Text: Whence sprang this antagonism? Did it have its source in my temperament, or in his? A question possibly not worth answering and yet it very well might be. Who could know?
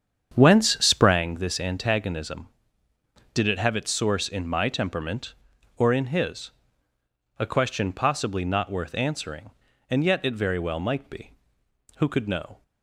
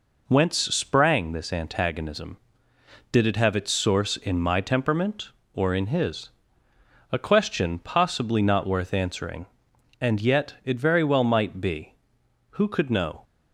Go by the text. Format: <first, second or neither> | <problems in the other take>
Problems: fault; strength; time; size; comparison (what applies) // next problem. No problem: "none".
second | starts louder than the rest; strong; until 1.2 s; 8 dB